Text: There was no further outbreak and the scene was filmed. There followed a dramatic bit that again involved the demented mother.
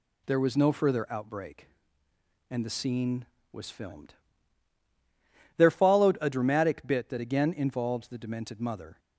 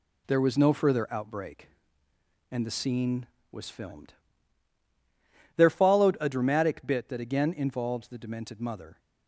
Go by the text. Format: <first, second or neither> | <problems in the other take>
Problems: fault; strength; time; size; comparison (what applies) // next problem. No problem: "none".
first | gets quieter; noticeable; throughout; 6 dB